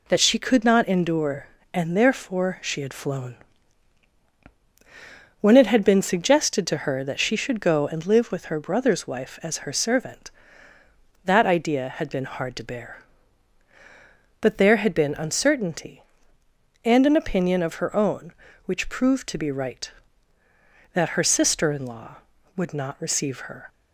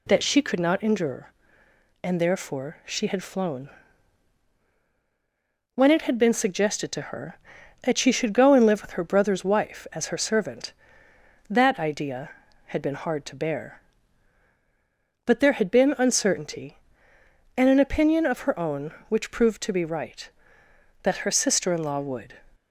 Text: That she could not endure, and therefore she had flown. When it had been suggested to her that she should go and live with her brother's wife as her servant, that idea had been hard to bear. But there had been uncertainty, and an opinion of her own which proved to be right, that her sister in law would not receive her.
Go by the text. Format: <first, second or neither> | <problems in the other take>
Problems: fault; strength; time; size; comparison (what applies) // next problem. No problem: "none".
first | stops before "not receive her"; at 22.5 s